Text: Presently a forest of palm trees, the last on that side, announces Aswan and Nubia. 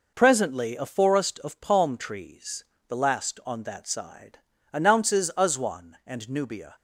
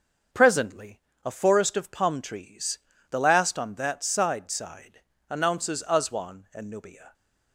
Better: first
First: none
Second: starts louder than the rest; until 1.5 s; 7 dB // pauses between "Presently" and "a"; slight; at 1.0 s; 0.24 s long // says "side" twice; at 4.4 s

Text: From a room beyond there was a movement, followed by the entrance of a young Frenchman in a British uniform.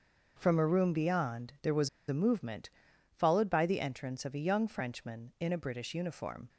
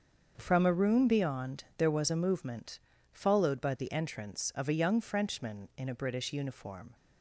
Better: second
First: starts louder than the rest; until 1.3 s; 6.5 dB // pauses between "was" and "a"; slight; at 1.8 s; 0.19 s long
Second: starts louder than the rest; until 1.3 s; 6.5 dB

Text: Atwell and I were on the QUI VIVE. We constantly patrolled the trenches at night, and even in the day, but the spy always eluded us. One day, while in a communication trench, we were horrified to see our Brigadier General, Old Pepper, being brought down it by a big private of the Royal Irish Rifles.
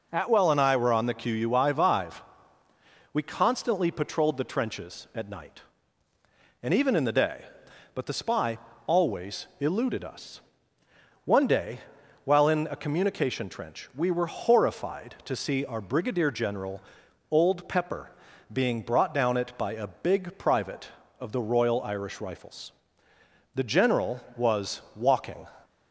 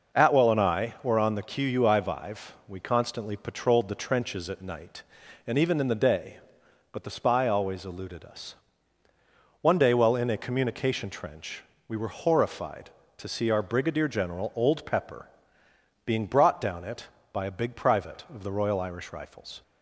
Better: second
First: pauses between "spy" and "always"; slight; at 8.5 s; 0.30 s long // goes on to say "The General was walking"; strong; from 23.5 s on; 1.9 s long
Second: none

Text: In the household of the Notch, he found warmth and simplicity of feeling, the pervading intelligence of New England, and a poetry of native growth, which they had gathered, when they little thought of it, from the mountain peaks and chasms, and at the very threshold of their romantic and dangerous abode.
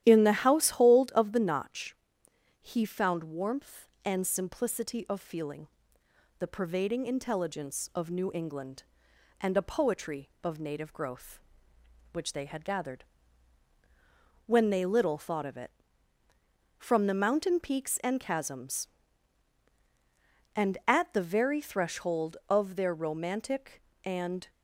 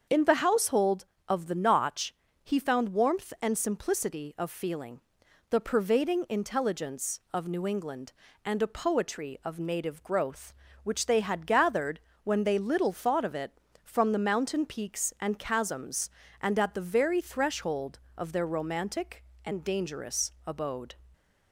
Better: second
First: starts louder than the rest; strong; until 1.0 s; 12 dB // stops before "dangerous abode"; at 24.4 s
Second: starts louder than the rest; strong; until 1.3 s; 7 dB

